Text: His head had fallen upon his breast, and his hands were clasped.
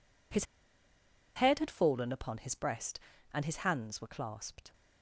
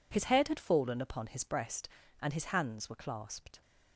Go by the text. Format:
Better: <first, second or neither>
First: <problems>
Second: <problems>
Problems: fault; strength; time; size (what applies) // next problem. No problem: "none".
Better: second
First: pauses between "His" and "head"; noticeable; at 0.4 s; 0.91 s long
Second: none